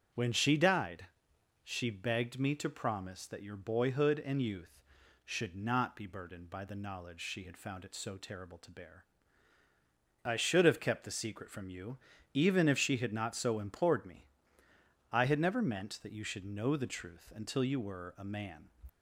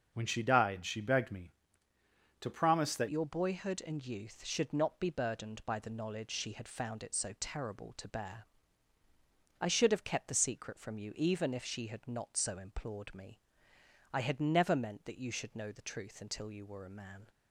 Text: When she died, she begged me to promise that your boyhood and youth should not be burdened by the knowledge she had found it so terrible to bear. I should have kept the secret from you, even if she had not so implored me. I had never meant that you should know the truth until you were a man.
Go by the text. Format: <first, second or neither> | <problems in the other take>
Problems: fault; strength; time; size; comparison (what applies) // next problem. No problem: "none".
first | starts louder than the rest; until 1.1 s; 6.5 dB; strong in the first // changes voice at "your"; from 3.0 s on; 14.2 s long